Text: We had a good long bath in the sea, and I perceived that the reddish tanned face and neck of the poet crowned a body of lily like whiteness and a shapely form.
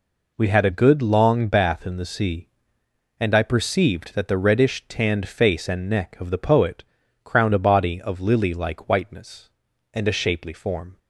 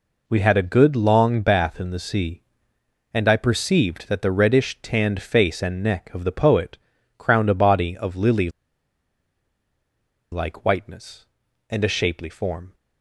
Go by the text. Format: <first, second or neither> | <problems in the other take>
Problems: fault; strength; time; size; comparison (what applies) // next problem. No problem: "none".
first | pauses between "poet" and "crowned"; at 6.7 s; 0.38 s long; also in the first // pauses between "lily" and "like"; strong; at 8.4 s; 1.8 s long